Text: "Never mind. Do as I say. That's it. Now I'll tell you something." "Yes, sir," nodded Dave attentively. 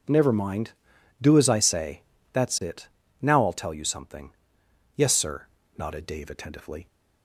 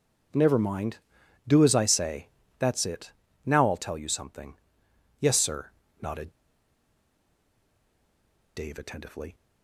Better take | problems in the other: first | pauses between "nodded" and "Dave"; strong; at 6.2 s; 2.2 s long

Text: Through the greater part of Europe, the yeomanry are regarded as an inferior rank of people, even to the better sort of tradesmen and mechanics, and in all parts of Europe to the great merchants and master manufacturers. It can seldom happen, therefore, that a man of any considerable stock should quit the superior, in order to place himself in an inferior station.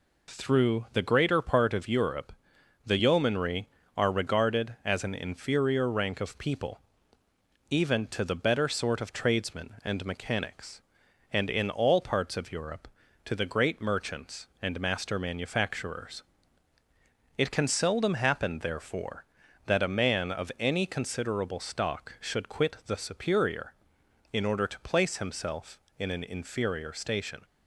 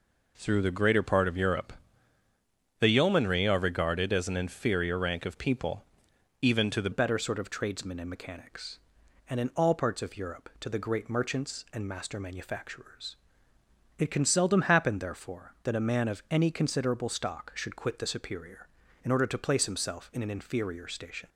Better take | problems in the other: first | changes voice at "better"; from 6.9 s on; 14.3 s long

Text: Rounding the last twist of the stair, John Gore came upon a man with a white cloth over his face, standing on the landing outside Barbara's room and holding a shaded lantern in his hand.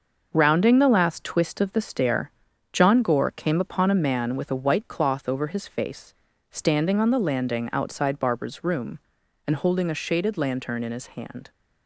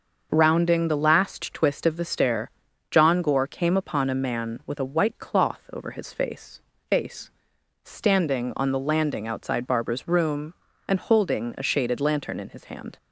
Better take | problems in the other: first | starts louder than the rest; until 1.3 s; 6.5 dB; noticeable in the first // says "face" twice; at 6.8 s

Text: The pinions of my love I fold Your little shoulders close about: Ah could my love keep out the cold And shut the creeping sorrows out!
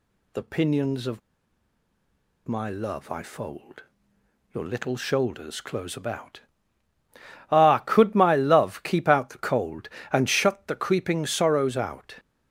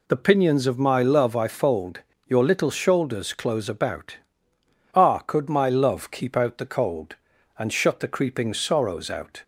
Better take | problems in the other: second | pauses between "of" and "my"; strong; at 1.2 s; 1.2 s long // pauses between "fold" and "Your"; noticeable; at 3.8 s; 0.68 s long; slight in the second

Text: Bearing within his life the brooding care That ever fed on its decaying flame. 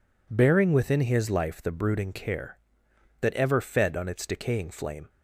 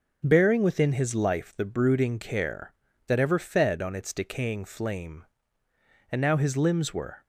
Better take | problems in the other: first | starts louder than the rest; until 1.2 s; 6.5 dB // goes on to say "And now his limbs were"; noticeable; from 6.0 s on; 1.1 s long

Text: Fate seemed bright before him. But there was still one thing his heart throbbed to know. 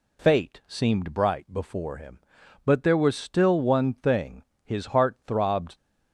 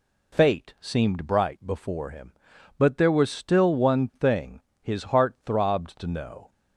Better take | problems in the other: second | pauses between "thing" and "his"; slight; at 4.4 s; 0.22 s long; slight in the second // stops before "to know"; at 5.7 s

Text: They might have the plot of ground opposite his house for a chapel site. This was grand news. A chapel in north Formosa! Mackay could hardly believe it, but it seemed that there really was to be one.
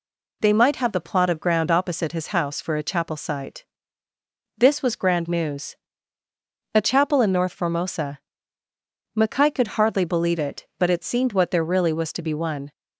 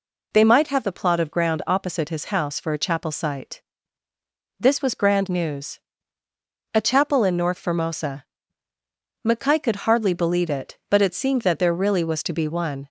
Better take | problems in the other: second | says "what" for "that"; at 11.3 s

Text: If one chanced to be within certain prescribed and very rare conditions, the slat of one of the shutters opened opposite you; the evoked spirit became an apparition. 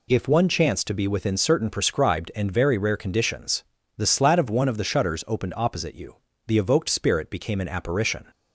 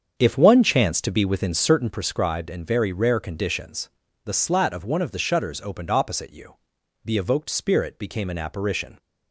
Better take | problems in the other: first | starts louder than the rest; strong; until 2.0 s; 7.5 dB

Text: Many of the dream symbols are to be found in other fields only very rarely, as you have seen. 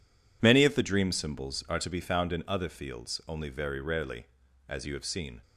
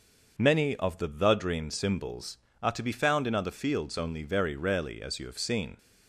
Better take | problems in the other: first | starts louder than the rest; until 1.4 s; 6 dB // says "the" twice; at 1.0 s

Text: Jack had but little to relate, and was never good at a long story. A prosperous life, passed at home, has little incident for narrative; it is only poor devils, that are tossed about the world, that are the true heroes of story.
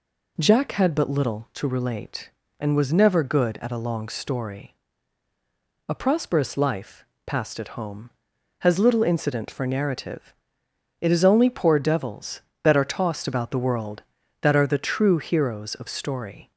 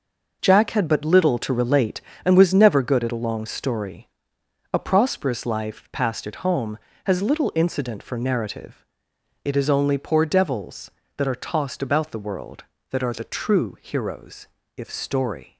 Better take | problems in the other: first | says "if" for "of"; at 14.7 s

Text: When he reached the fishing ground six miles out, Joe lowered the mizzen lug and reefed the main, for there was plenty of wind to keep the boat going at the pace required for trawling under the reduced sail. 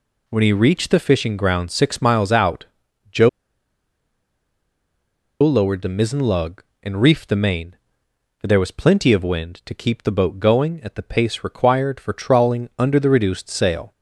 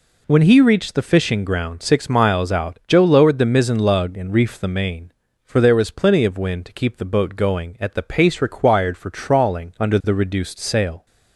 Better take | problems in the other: second | pauses between "Joe" and "lowered"; strong; at 3.2 s; 2.1 s long

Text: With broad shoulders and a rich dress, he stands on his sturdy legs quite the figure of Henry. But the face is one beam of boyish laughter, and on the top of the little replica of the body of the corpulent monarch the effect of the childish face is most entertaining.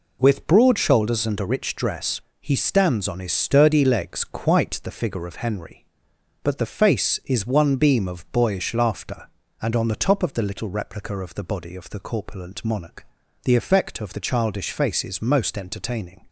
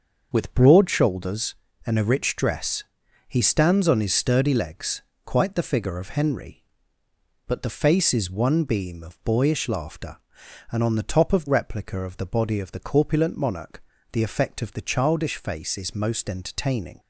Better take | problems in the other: first | starts louder than the rest; until 1.3 s; 6.5 dB // pauses between "legs" and "quite"; slight; at 5.0 s; 0.24 s long // skips "the little"; at 11.4 s // pauses between "monarch" and "the"; slight; at 13.8 s; 0.30 s long; also in the first

